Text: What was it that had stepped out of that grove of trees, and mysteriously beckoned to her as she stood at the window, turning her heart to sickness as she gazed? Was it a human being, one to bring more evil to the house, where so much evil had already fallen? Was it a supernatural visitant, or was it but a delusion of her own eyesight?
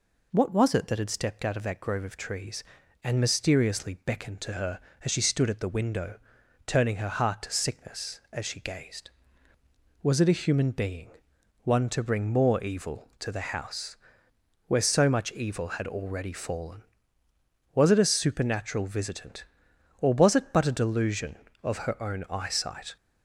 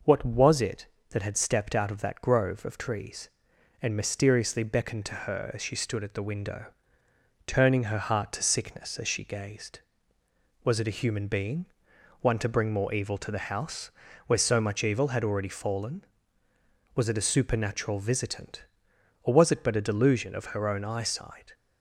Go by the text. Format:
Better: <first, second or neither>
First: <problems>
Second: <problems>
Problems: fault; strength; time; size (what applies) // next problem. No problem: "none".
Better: neither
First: none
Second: none